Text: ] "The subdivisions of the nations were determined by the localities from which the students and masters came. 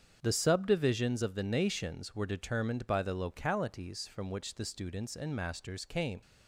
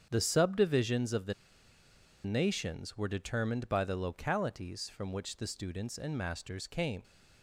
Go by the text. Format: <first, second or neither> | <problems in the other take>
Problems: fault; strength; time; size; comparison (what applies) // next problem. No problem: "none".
first | starts louder than the rest; strong; until 1.1 s; 7.5 dB; strong in the first // pauses between "the" and "nations"; noticeable; at 1.3 s; 0.91 s long